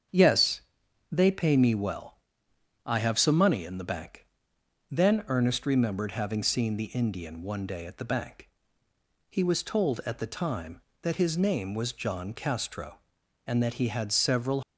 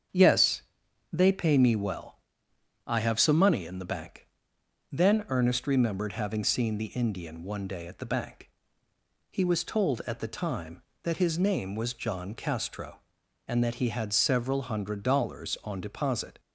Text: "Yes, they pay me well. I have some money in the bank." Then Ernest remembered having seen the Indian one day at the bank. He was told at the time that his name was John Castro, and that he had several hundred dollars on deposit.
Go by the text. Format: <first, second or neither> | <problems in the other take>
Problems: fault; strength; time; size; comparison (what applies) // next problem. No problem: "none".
second | starts louder than the rest; strong; until 1.6 s; 7.5 dB; strong in the second // stops before "hundred dollars on deposit"; at 14.6 s